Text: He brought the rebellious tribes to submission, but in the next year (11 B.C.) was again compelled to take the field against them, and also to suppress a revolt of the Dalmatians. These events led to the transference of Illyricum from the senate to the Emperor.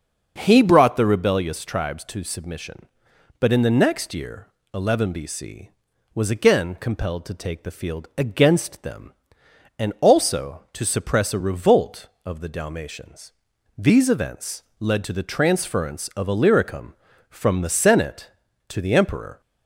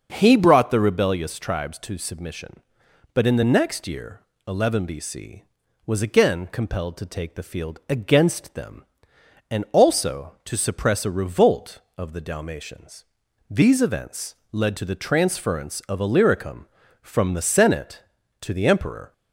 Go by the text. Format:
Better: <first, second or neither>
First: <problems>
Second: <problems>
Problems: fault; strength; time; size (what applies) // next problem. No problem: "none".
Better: neither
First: starts louder than the rest; until 1.3 s; 6.5 dB // pauses between "events" and "led"; slight; at 14.6 s; 0.16 s long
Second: starts louder than the rest; until 1.1 s; 6.5 dB // pauses between "events" and "led"; slight; at 14.3 s; 0.16 s long